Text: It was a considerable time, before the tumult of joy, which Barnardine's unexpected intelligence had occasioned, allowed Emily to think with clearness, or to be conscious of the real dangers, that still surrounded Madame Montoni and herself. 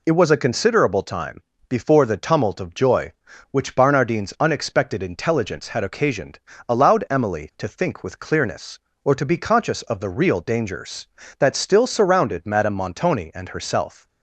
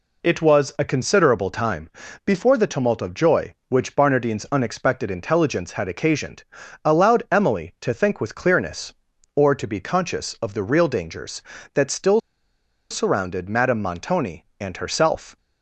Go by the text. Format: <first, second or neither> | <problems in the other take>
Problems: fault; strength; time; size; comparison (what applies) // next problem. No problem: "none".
first | pauses between "still" and "surrounded"; noticeable; at 12.2 s; 0.70 s long